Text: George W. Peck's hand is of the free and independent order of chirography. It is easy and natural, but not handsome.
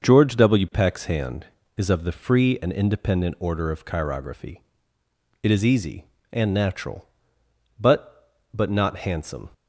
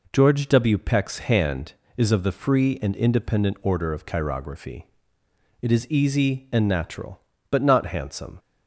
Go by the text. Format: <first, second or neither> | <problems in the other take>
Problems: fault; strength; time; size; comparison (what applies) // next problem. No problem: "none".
second | starts louder than the rest; until 1.0 s; 6 dB // says "but" twice; at 8.5 s